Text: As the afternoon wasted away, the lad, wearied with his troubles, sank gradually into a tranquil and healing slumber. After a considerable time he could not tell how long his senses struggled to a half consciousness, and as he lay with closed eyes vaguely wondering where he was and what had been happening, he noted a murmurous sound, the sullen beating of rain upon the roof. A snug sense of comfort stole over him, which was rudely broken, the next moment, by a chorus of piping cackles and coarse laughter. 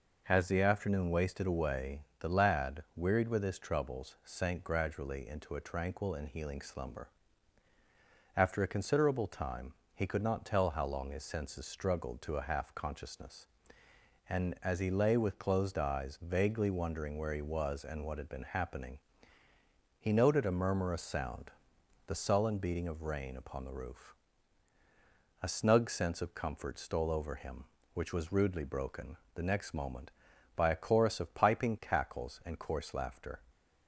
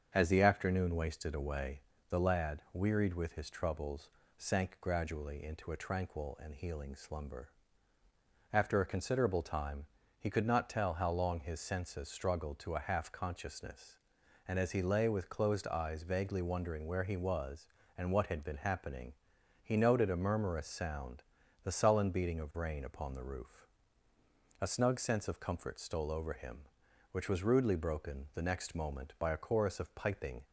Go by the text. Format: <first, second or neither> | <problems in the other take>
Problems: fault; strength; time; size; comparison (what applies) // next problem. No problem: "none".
first | starts louder than the rest; until 1.1 s; 7 dB // pauses between "time" and "he"; slight; at 9.8 s; 0.34 s long; slight in the first // stops before "cackles and coarse laughter"; at 30.4 s